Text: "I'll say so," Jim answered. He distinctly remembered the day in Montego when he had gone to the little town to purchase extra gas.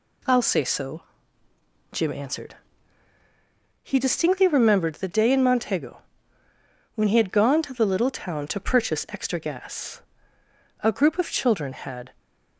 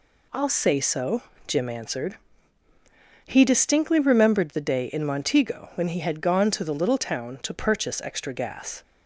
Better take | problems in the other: second | pauses between "Montego" and "when"; noticeable; at 6.0 s; 0.94 s long // goes on to say "A group of children had"; from 10.8 s on; 1.3 s long

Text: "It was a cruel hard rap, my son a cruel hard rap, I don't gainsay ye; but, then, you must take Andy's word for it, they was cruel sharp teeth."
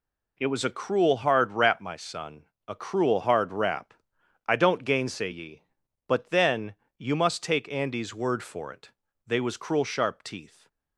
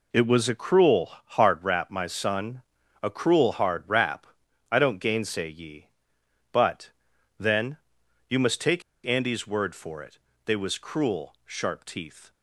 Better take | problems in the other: first | pauses between "son" and "a"; at 2.6 s; 0.38 s long; slight in the first // pauses between "take" and "Andy's"; slight; at 8.8 s; 0.23 s long

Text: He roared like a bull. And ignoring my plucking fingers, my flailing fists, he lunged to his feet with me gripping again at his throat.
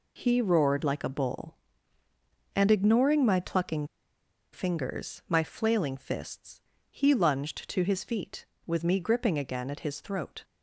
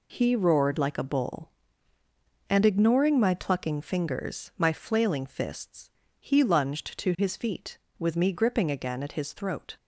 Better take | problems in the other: second | pauses between "plucking" and "fingers"; noticeable; at 3.8 s; 0.67 s long

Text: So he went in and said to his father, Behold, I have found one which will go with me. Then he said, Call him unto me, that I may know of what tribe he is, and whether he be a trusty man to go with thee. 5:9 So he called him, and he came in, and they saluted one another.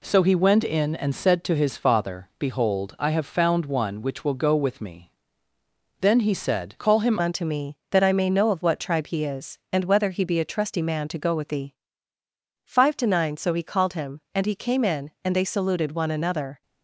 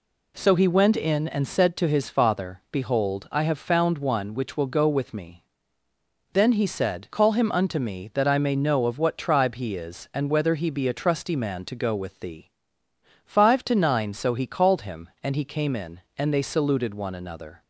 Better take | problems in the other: second | changes voice at "unto"; from 7.1 s on; 9.5 s long

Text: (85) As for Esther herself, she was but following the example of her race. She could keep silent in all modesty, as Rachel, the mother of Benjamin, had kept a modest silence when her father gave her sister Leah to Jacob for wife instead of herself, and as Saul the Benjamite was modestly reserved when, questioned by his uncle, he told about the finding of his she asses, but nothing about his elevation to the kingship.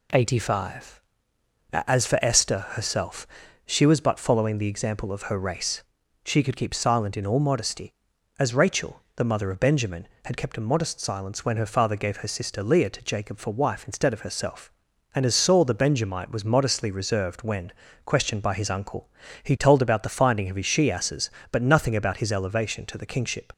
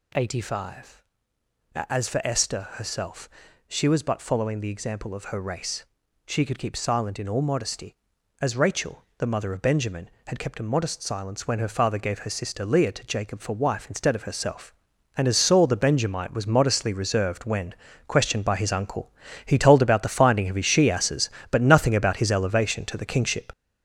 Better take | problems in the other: first | gets louder; throughout; 7 dB

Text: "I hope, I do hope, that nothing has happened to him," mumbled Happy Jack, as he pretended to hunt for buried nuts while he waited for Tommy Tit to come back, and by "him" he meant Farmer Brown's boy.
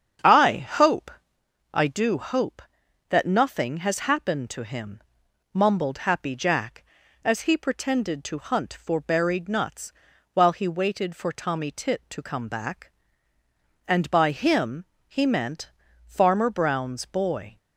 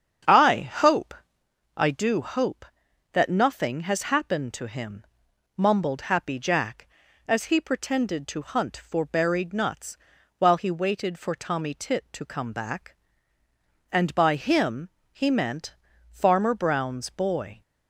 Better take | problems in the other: neither | starts louder than the rest; strong; the same in both // pauses between "nuts" and "while"; the same in both // pauses between "him" and "he"; slight; the same in both // pauses between "meant" and "Farmer"; the same in both

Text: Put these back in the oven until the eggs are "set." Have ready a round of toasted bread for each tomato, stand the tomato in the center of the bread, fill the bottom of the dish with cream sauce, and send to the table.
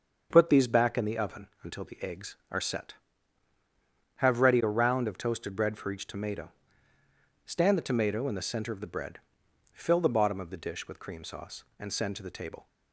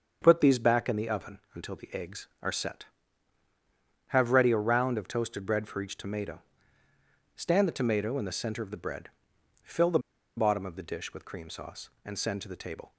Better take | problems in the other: first | starts louder than the rest; until 1.2 s; 7 dB; also in the first // pauses between "the" and "bottom"; at 9.9 s; 0.38 s long

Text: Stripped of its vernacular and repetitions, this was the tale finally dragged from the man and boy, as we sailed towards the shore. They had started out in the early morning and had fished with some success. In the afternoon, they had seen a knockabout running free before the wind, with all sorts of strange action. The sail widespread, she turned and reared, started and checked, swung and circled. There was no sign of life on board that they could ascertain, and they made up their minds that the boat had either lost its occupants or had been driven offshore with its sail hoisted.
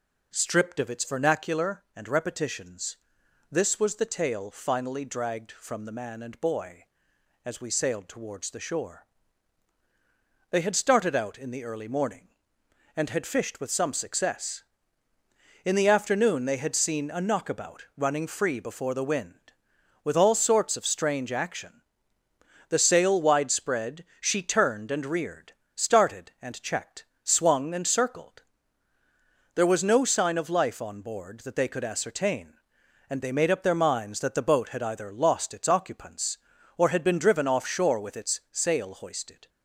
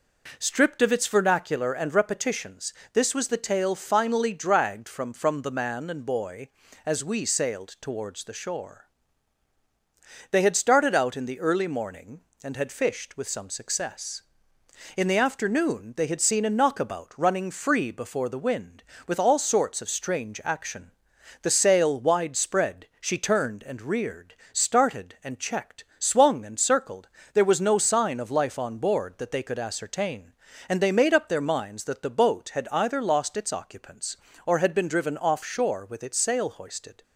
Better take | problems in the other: first | says "from" twice; at 5.1 s

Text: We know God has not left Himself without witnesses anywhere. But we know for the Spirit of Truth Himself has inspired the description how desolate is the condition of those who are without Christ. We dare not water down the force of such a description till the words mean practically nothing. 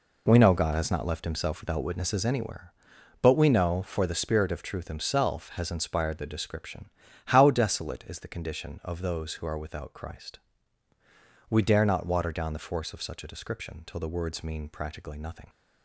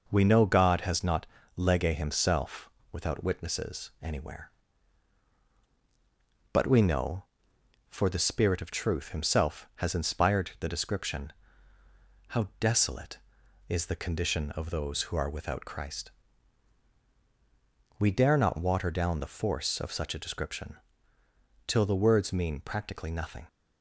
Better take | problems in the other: first | says "lege" for "left"; at 1.5 s // pauses between "Himself" and "without"; slight; at 2.6 s; 0.22 s long // pauses between "description" and "how"; noticeable; at 11.3 s; 0.94 s long; also in the first // pauses between "description" and "till"; noticeable; at 20.7 s; 0.90 s long

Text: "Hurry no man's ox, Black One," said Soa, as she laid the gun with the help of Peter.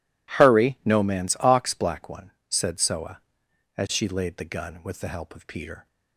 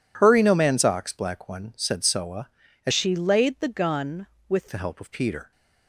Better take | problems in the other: first | changes voice from "she" to "with"; from 2.9 to 4.6 s; 1.7 s long

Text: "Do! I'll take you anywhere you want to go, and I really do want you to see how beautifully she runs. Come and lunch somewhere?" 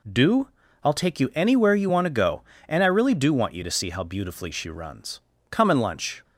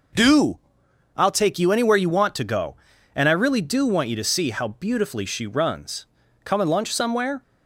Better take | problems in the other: second | stops before "somewhere"; at 6.2 s

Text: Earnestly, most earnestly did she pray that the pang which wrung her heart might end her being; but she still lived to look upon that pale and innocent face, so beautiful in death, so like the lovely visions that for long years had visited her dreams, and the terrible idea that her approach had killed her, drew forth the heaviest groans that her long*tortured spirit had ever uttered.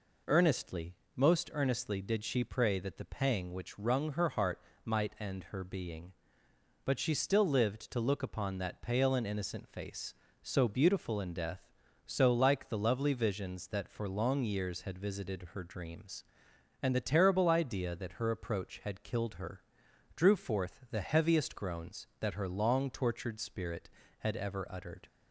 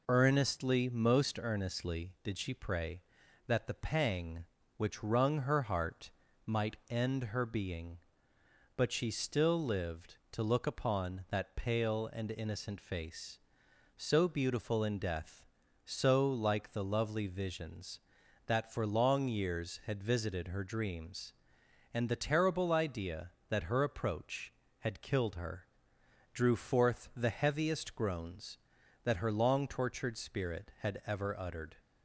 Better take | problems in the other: neither | pauses between "heart" and "might"; slight; the same in both

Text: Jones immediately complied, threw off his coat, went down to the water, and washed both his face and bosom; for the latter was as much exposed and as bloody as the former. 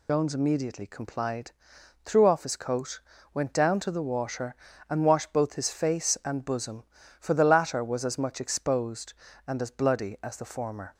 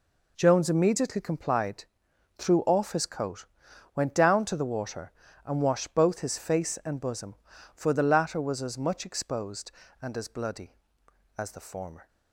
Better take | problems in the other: second | loses the start of "Jones"; at 0.0 s; 85 ms

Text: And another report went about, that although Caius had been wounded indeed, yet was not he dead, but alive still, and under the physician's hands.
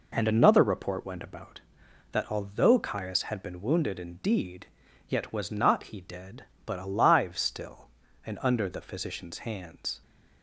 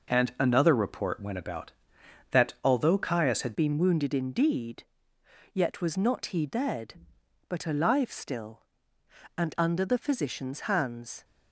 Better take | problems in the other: first | changes voice at "been"; from 3.5 s on; 7.7 s long

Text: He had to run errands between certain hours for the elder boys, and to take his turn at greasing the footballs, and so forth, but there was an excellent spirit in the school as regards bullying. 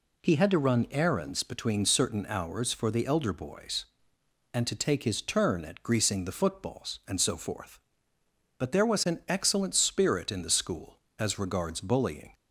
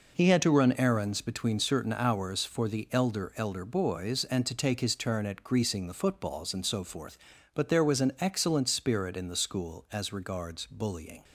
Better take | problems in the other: first | says "elder" twice; at 3.3 s

